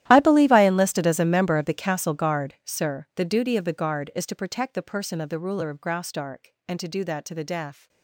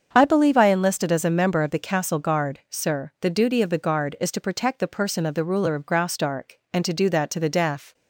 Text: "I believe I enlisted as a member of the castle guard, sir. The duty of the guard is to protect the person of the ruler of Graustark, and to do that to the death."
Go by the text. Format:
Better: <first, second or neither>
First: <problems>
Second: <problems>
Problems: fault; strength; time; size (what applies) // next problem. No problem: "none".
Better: second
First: gets quieter; strong; throughout; 19 dB // starts louder than the rest; strong; until 1.0 s; 13 dB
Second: starts louder than the rest; until 1.1 s; 7 dB